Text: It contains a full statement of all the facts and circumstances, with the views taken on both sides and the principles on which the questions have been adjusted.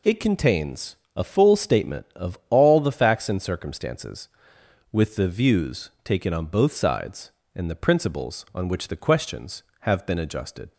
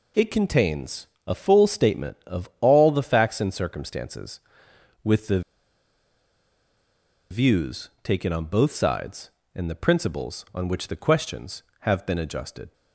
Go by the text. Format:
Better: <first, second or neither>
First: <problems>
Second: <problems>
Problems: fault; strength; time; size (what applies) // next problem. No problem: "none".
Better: first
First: pauses between "contains" and "a"; slight; at 0.9 s; 0.20 s long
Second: pauses between "contains" and "a"; slight; at 1.0 s; 0.20 s long // pauses between "the" and "views"; strong; at 5.4 s; 1.8 s long